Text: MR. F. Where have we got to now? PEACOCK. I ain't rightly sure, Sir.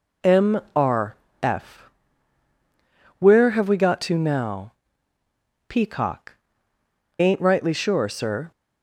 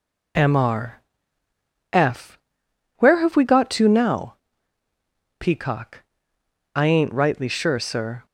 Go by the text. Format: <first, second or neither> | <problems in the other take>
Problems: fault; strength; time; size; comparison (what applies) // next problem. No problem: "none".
second | skips "I"; at 6.7 s